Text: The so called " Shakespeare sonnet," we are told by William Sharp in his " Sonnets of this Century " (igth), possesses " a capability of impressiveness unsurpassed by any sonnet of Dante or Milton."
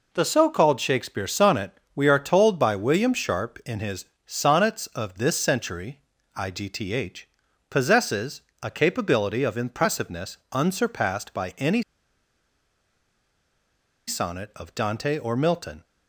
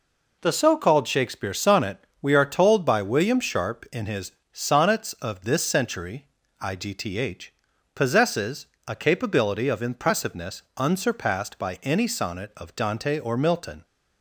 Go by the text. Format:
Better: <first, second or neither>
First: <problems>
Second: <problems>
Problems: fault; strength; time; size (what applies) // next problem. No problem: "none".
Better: second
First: pauses between "any" and "sonnet"; strong; at 11.8 s; 2.2 s long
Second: none